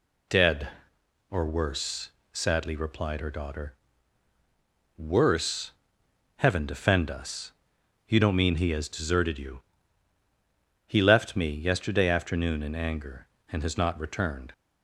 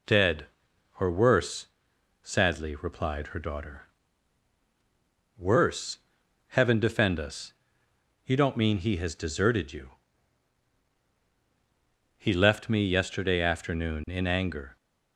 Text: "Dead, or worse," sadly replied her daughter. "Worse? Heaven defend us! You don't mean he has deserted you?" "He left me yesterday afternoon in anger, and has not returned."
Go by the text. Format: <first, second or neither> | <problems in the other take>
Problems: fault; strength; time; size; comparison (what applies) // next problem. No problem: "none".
first | stops before "and has not returned"; at 14.7 s